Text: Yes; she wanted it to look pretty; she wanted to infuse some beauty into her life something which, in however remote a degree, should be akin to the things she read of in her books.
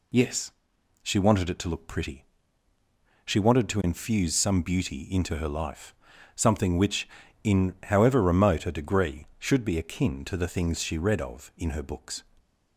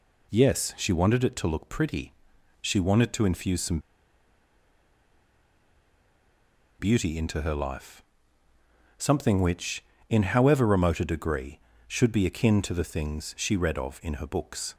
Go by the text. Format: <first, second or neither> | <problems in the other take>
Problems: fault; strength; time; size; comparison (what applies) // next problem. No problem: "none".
first | pauses between "some" and "beauty"; strong; at 3.7 s; 3.0 s long // pauses between "life" and "something"; noticeable; at 8.0 s; 0.96 s long; also in the first